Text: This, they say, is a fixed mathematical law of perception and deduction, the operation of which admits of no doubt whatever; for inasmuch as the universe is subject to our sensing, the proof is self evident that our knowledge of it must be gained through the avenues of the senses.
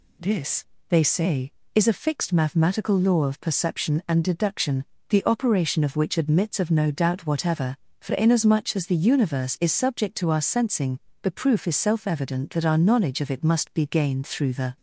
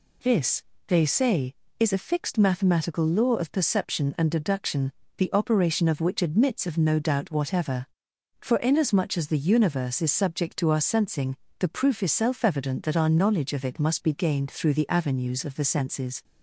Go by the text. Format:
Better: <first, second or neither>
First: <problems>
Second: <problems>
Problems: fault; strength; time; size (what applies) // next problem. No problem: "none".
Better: second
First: stops before "avenues of the senses"; at 14.7 s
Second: none